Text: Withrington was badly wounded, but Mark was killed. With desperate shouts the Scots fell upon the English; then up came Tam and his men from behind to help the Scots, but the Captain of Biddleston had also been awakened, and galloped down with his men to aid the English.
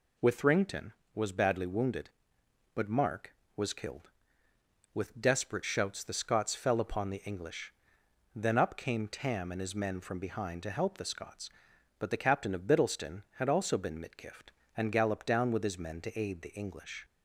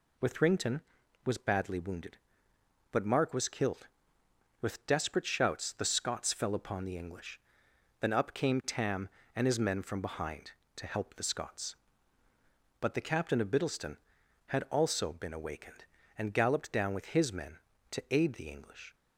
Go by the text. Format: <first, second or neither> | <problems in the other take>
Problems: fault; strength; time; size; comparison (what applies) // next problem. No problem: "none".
second | says "mitgift" for "awakened"; at 13.9 s